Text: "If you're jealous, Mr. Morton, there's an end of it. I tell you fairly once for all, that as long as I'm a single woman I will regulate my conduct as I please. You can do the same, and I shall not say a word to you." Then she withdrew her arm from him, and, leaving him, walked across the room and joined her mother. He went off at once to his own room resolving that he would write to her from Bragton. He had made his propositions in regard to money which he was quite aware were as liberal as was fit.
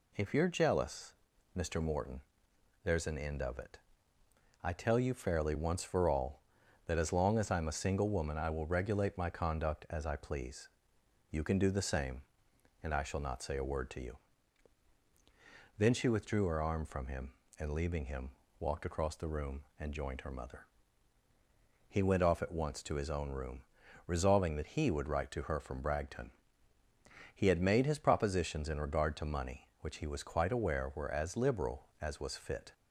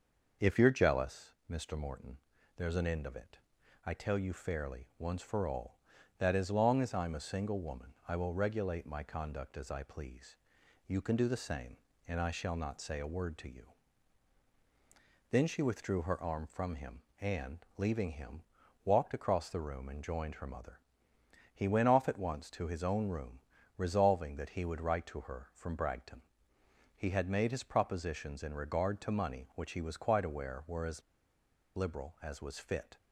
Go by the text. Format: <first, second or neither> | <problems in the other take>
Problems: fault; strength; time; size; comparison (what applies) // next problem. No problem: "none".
first | starts louder than the rest; noticeable; until 1.5 s; 6 dB // pauses between "room" and "resolving"; at 23.3 s; 0.38 s long; also in the first // pauses between "as" and "liberal"; noticeable; at 31.0 s; 0.74 s long